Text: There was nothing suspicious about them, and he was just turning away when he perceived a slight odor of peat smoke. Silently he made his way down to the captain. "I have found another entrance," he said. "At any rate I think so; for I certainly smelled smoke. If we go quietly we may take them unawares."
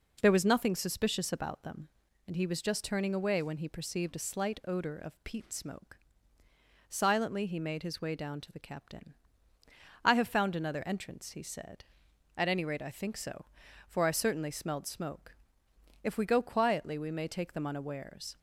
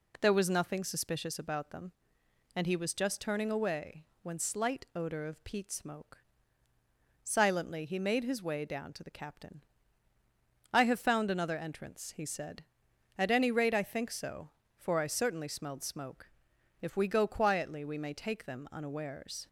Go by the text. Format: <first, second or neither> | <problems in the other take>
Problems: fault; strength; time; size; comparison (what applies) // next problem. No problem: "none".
first | pauses between "away" and "when"; slight; at 4.0 s; 0.16 s long // skips "he perceived a"; at 4.3 s